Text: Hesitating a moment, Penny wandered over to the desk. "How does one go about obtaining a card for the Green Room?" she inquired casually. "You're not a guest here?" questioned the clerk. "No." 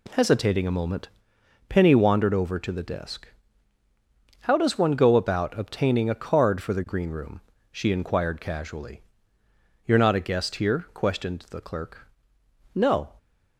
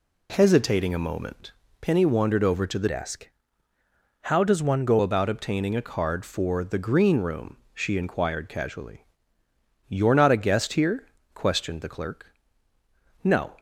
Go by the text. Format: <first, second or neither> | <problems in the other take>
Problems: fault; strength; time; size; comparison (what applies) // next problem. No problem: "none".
first | changes voice from "desk" to "go"; from 2.8 to 4.9 s; 2.1 s long